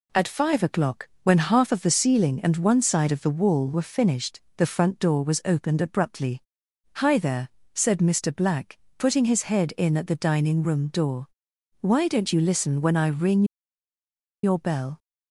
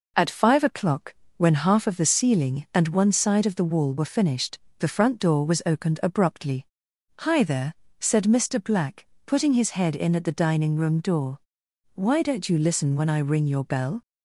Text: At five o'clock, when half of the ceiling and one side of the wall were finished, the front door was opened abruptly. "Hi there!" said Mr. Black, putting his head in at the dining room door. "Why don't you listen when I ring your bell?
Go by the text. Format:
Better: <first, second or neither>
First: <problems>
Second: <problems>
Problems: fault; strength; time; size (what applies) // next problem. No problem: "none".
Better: second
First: pauses between "ring" and "your"; at 13.4 s; 0.99 s long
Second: none